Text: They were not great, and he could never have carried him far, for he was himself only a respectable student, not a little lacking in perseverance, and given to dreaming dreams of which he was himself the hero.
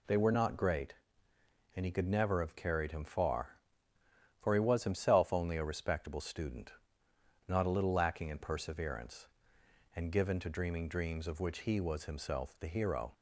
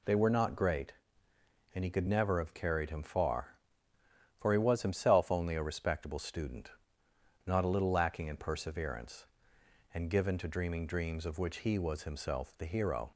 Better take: neither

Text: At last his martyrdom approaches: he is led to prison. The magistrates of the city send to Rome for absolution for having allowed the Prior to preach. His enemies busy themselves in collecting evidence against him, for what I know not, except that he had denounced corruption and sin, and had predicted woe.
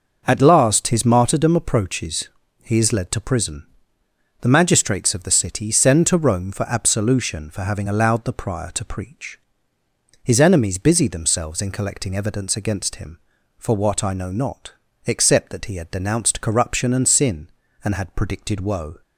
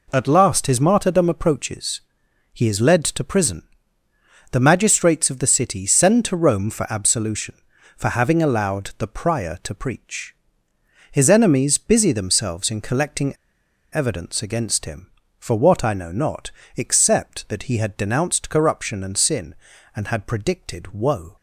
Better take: first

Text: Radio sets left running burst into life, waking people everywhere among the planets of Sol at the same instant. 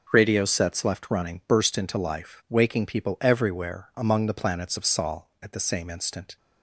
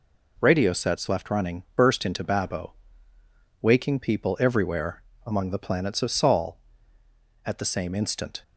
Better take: first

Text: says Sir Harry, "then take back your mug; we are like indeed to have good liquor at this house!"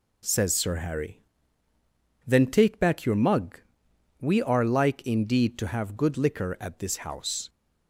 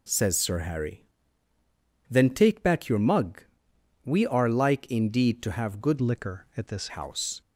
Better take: first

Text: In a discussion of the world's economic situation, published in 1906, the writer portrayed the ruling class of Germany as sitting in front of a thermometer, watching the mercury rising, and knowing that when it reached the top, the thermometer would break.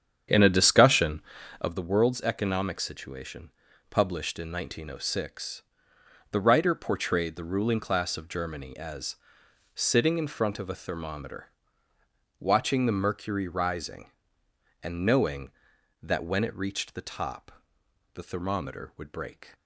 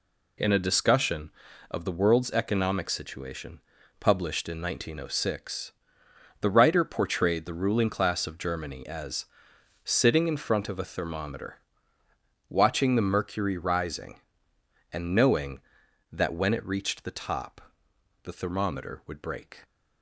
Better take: second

